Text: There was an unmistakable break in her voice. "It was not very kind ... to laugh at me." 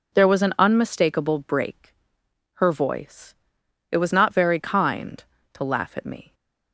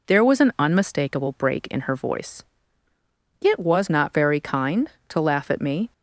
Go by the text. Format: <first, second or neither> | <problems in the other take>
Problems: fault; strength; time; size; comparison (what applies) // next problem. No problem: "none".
second | skips "in"; at 2.2 s